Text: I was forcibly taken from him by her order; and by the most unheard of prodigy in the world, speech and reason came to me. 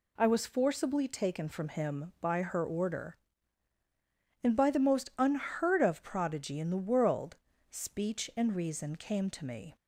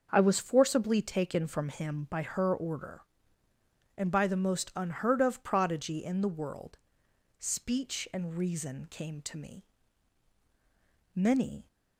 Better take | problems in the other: first | starts louder than the rest; until 1.1 s; 6.5 dB // goes on to say "Many"; from 11.1 s on; 0.54 s long

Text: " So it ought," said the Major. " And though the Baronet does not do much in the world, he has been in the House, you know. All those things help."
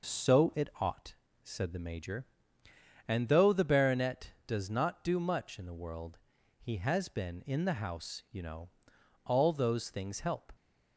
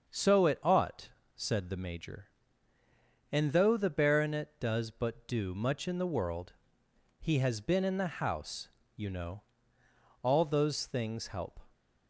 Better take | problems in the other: first | says "but" for "not"; at 4.8 s

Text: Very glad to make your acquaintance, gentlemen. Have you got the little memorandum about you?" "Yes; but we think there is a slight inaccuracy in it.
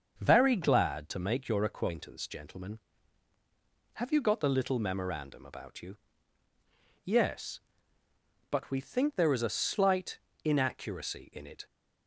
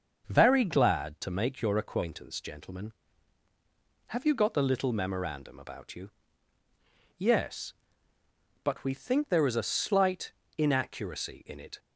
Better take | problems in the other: neither | starts louder than the rest; the same in both // pauses between "slight" and "inaccuracy"; slight; the same in both

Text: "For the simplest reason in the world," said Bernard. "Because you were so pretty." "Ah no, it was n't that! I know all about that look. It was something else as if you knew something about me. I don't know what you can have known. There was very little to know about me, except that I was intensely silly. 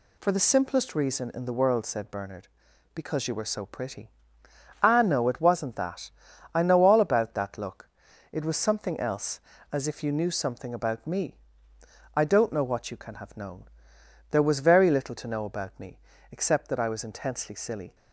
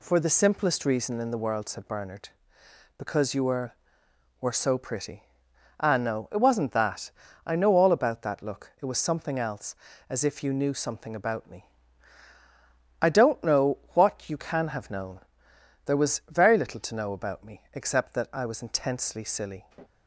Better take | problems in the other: first | says "were" twice; at 4.3 s // pauses between "know" and "what"; slight; at 13.7 s; 0.16 s long

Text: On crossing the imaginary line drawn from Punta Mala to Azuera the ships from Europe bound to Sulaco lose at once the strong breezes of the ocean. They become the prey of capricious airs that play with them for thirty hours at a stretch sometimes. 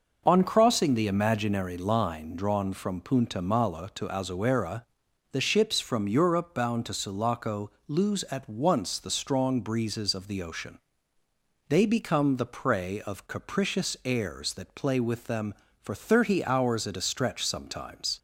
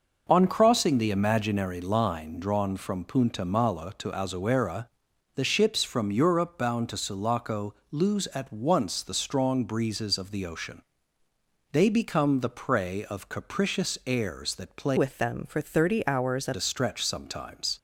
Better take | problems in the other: first | pauses between "Azuera" and "the"; noticeable; at 4.8 s; 0.48 s long; noticeable in the first // pauses between "Sulaco" and "lose"; slight; at 7.7 s; 0.18 s long; slight in the first // changes voice from "with" to "at"; from 14.9 to 16.5 s; 1.6 s long

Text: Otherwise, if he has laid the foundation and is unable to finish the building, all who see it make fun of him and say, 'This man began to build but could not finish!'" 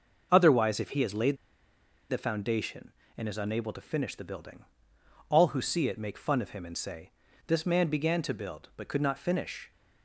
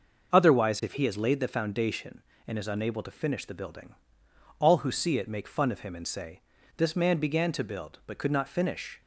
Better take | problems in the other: second | pauses between "laid" and "the"; noticeable; at 1.3 s; 0.74 s long

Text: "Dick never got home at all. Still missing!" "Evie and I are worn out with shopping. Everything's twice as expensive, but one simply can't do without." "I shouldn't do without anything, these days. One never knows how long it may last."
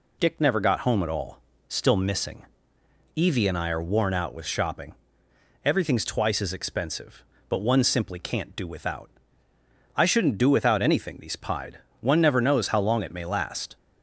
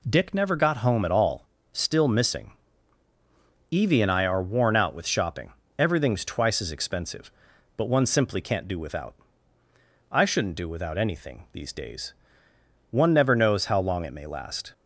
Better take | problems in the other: second | says "pied" for "days"; at 11.3 s

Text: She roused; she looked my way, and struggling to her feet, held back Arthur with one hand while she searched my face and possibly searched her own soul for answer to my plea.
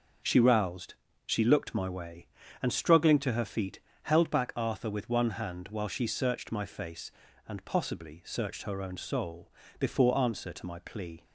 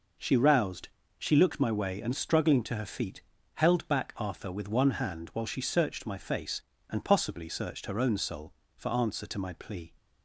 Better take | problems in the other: second | starts louder than the rest; noticeable; until 1.5 s; 6 dB // says "before" for "for"; at 9.7 s

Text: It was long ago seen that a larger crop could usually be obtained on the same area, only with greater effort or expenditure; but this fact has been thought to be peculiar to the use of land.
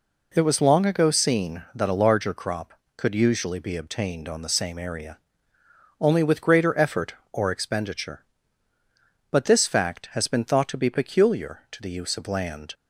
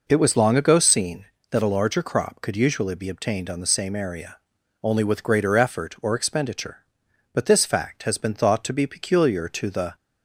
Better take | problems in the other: first | stops before "use of land"; at 9.9 s

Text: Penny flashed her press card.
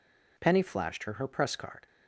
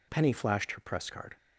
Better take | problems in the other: second | says "her" twice; at 1.1 s

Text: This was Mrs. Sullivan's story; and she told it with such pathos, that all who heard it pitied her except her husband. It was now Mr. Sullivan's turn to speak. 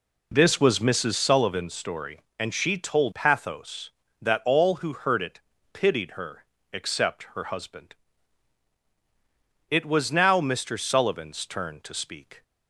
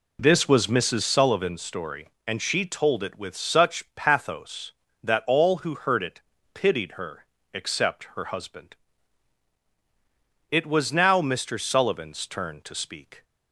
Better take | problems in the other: second | skips "it with such"; at 3.1 s // pauses between "it" and "pitied"; slight; at 5.3 s; 0.34 s long; slight in the second // pauses between "her" and "except"; slight; at 6.4 s; 0.30 s long; slight in the second

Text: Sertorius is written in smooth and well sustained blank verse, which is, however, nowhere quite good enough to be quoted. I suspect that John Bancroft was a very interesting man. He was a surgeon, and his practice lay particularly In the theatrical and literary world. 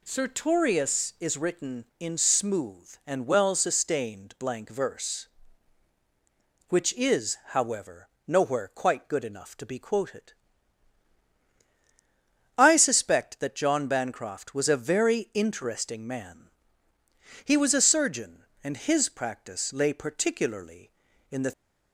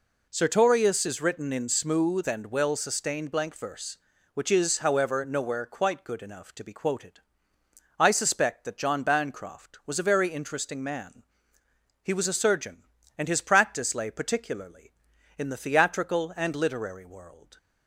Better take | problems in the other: second | stops before "theatrical and literary world"; at 21.5 s

